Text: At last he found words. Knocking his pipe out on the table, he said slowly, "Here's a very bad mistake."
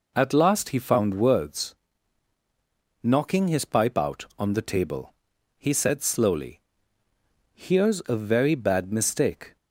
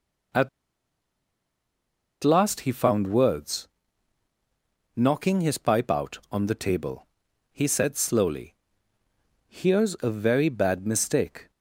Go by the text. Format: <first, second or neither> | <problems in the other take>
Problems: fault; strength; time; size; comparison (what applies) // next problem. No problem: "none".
first | pauses between "At" and "last"; strong; at 0.4 s; 1.7 s long